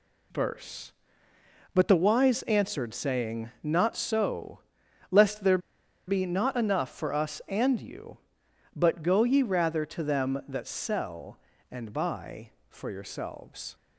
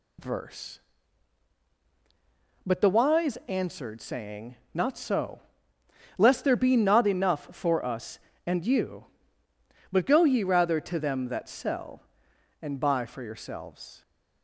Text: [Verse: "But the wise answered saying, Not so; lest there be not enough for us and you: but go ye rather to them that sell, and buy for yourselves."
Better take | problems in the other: second | pauses between "there" and "be"; noticeable; at 5.5 s; 0.49 s long

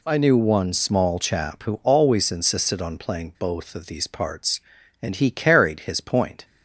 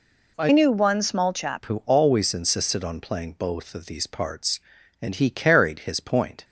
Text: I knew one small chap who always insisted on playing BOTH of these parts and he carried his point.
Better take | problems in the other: first | changes voice from "knew" to "chap"; from 0.5 to 1.6 s; 1.1 s long

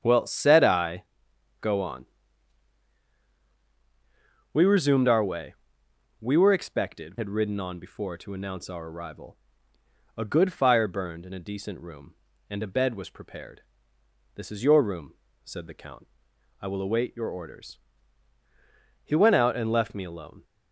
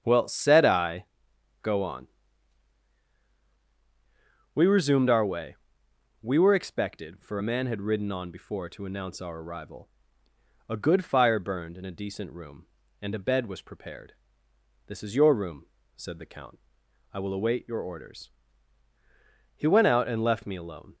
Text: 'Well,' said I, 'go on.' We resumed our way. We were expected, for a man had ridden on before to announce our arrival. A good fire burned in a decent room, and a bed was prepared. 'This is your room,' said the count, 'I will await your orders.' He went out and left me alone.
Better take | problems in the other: second | starts louder than the rest; strong; until 1.0 s; 8.5 dB; strong in the second // skips "for a man"; at 7.1 s

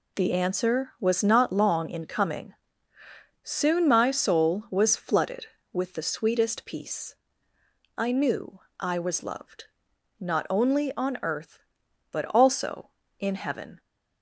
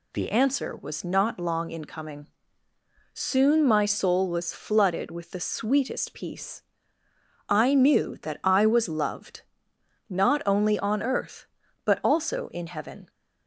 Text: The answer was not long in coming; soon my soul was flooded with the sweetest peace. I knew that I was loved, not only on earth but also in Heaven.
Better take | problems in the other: second | skips "that"; at 8.6 s

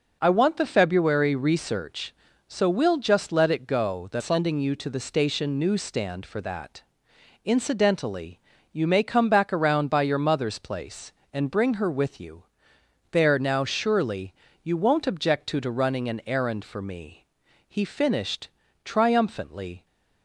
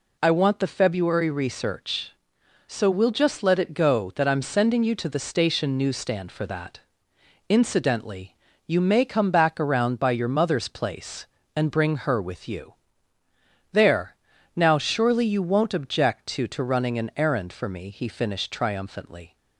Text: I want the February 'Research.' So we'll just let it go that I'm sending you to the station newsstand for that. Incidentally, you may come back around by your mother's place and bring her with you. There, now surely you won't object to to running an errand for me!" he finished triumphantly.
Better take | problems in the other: second | skips "I'm"; at 4.2 s // pauses between "surely" and "you"; slight; at 14.3 s; 0.30 s long // pauses between "finished" and "triumphantly"; slight; at 18.4 s; 0.34 s long

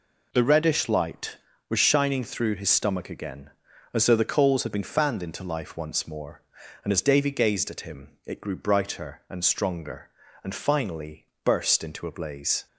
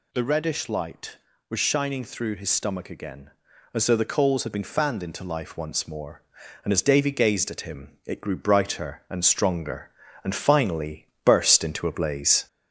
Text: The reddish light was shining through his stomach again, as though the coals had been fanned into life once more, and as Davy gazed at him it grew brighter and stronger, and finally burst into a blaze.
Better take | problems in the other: first | gets louder; slight; throughout; 2.5 dB // pauses between "finally" and "burst"; slight; at 11.0 s; 0.18 s long; slight in the first

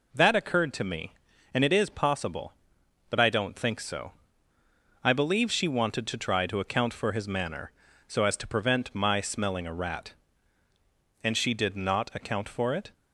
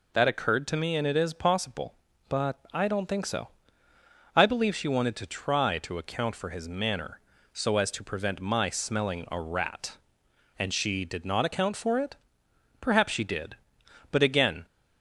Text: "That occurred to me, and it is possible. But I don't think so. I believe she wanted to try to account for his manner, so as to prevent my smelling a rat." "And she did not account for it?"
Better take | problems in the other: first | goes on to say "Perhaps she did but again"; strong; from 12.8 s on; 1.8 s long

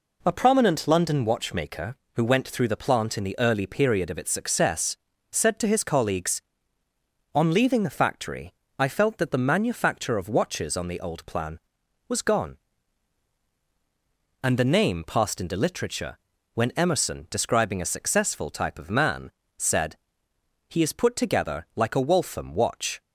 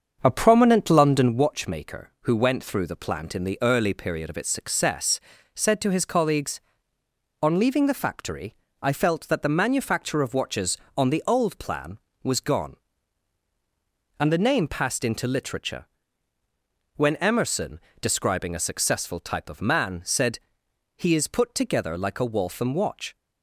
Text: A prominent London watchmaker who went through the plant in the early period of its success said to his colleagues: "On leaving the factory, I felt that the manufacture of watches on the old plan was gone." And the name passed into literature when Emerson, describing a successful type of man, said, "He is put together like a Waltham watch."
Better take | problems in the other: first | starts louder than the rest; until 1.5 s; 7 dB // pauses between "success" and "said"; slight; at 5.1 s; 0.36 s long; slight in the first // pauses between "literature" and "when"; at 15.8 s; 1.1 s long; slight in the first

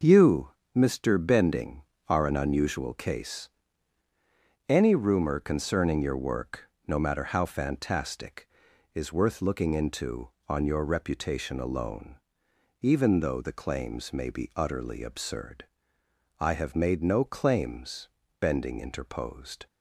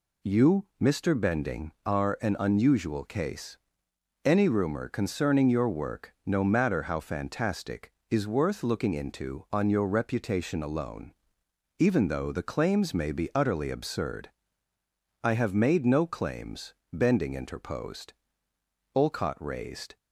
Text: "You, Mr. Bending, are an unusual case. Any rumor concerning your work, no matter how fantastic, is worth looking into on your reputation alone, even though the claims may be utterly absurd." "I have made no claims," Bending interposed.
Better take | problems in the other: first | goes on to say "Olcott raised"; noticeable; from 18.9 s on; 1.0 s long

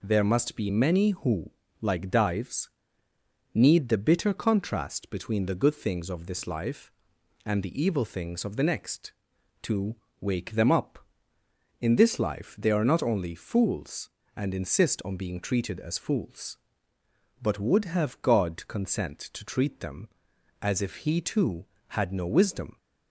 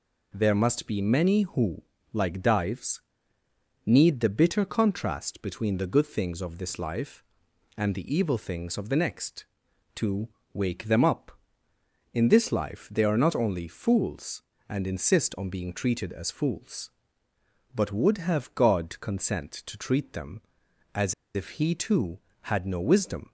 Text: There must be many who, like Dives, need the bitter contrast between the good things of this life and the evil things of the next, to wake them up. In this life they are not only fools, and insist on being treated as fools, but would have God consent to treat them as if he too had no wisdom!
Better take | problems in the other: first | pauses between "to" and "wake"; slight; at 10.2 s; 0.26 s long; slight in the first // pauses between "as" and "if"; slight; at 21.1 s; 0.21 s long

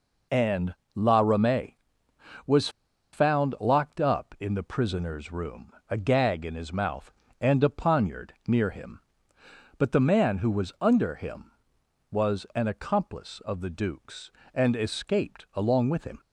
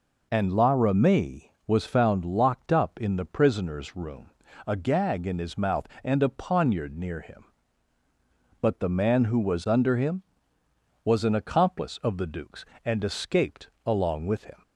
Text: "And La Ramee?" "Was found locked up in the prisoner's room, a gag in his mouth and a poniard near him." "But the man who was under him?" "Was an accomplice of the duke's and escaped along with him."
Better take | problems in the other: second | pauses between "And" and "La"; slight; at 0.7 s; 0.20 s long // pauses between "Was" and "found"; at 2.6 s; 0.44 s long

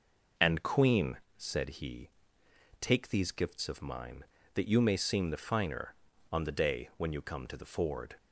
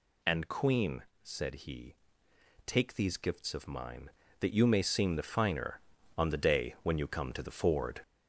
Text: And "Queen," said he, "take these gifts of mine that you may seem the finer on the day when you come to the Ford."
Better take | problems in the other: first | gets louder; noticeable; throughout; 5 dB

